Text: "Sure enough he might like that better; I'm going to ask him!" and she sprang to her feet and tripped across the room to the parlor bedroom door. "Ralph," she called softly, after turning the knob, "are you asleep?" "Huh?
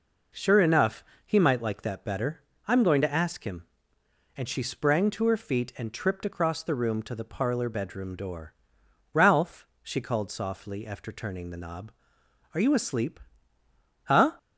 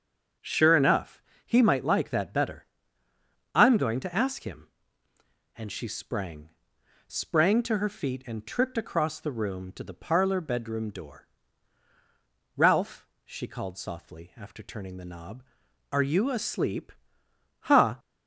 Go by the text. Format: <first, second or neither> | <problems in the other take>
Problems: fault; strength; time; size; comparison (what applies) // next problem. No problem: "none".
first | starts louder than the rest; until 1.6 s; 7 dB // pauses between "enough" and "he"; slight; at 1.2 s; 0.24 s long; slight in the first // says "sprang" twice; at 7.0 s